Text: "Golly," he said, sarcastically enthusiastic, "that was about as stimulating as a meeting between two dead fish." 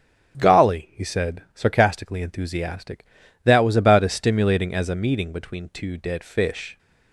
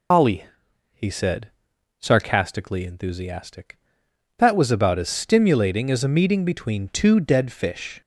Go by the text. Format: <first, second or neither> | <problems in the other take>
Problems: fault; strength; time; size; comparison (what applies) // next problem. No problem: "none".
first | loses the start of "Golly"; at 0.1 s; 115 ms